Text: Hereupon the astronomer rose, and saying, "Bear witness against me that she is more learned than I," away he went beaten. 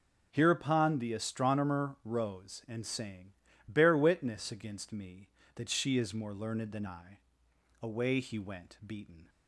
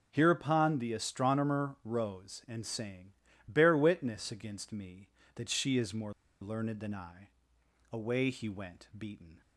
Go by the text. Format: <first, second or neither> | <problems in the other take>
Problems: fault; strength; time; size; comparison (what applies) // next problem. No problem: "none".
first | pauses between "more" and "learned"; slight; at 6.1 s; 0.28 s long